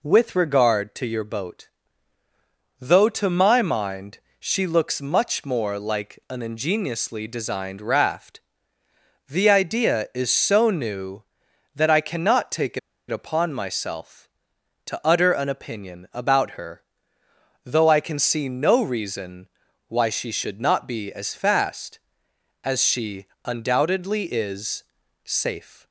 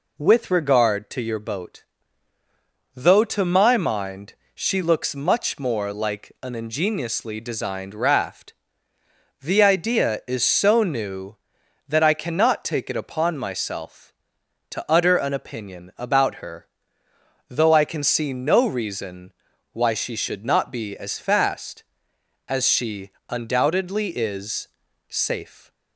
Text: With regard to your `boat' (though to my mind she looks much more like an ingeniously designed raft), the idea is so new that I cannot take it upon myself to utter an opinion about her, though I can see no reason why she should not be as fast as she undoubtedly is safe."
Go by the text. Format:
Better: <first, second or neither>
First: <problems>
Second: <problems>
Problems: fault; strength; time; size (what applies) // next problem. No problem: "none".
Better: second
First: pauses between "mind" and "she"; slight; at 4.1 s; 0.22 s long // pauses between "it" and "upon"; slight; at 12.7 s; 0.30 s long // pauses between "reason" and "why"; at 19.4 s; 0.40 s long // pauses between "she" and "undoubtedly"; slight; at 23.2 s; 0.20 s long // pauses between "is" and "safe"; at 24.8 s; 0.40 s long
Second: pauses between "mind" and "she"; slight; at 4.3 s; 0.22 s long // pauses between "reason" and "why"; at 19.3 s; 0.40 s long // pauses between "she" and "undoubtedly"; slight; at 23.1 s; 0.20 s long // pauses between "is" and "safe"; at 24.6 s; 0.40 s long